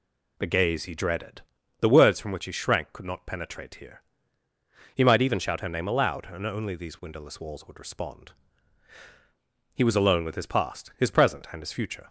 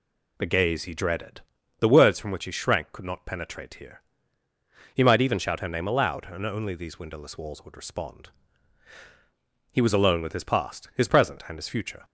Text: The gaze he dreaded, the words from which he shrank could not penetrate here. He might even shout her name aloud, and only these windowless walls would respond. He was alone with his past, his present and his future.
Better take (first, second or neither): neither